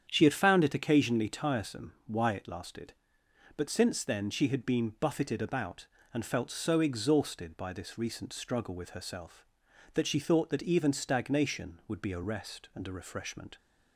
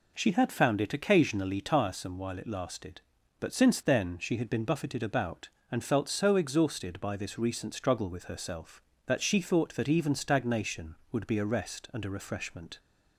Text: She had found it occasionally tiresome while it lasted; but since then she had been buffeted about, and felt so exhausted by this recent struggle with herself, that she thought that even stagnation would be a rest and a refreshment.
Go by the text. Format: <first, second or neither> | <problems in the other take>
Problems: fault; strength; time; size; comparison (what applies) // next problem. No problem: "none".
second | starts louder than the rest; strong; until 1.1 s; 8.5 dB // says "why" for "while"; at 2.0 s